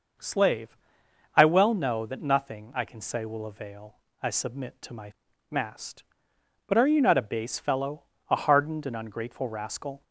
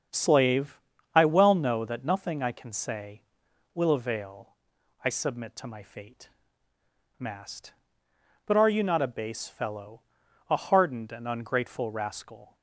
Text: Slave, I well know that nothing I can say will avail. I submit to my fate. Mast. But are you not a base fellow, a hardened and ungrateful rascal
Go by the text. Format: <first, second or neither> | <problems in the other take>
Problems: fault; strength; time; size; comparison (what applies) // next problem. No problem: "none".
second | starts louder than the rest; noticeable; until 1.8 s; 6 dB; also in the second // skips "fate"; at 5.3 s